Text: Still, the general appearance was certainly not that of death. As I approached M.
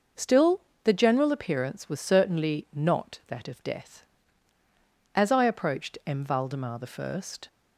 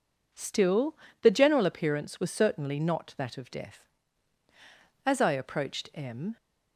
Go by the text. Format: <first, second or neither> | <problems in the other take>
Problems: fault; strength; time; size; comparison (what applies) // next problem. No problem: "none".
second | goes on to say "Valdemar I"; noticeable; from 6.2 s on; 0.98 s long